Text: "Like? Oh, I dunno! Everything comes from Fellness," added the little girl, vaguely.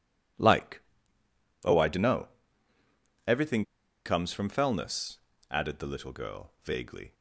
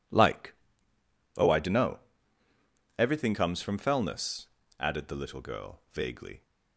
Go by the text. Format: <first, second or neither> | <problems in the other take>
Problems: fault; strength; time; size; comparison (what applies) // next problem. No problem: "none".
second | pauses between "Everything" and "comes"; at 3.6 s; 0.42 s long